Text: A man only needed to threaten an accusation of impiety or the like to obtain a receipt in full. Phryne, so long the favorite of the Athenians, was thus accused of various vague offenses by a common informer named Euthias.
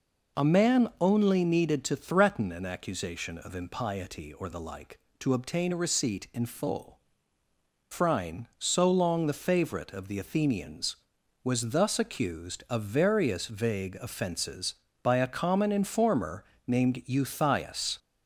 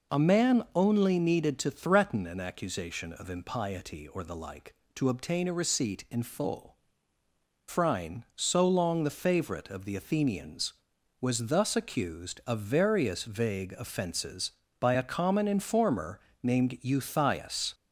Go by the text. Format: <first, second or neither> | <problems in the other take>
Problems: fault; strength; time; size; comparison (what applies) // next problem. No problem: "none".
neither | pauses between "informer" and "named"; slight; the same in both